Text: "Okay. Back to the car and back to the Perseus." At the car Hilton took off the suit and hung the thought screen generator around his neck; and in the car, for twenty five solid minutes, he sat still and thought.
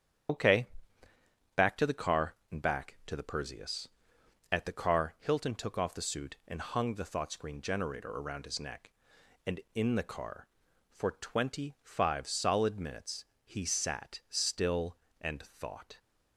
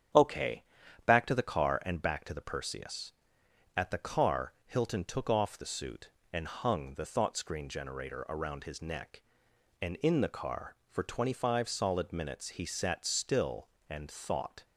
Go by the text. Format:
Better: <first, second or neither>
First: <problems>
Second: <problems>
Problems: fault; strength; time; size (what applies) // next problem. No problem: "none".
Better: second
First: loses the start of "Okay"; at 0.2 s; 70 ms // starts louder than the rest; strong; until 2.2 s; 9.5 dB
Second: starts louder than the rest; strong; until 1.6 s; 9 dB